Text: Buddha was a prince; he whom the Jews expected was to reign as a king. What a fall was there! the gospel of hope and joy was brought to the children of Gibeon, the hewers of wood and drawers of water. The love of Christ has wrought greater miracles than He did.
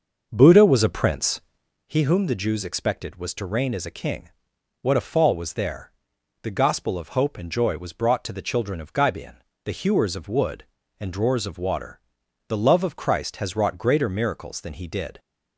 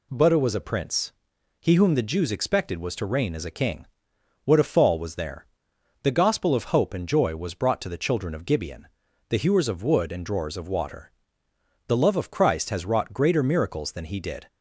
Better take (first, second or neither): second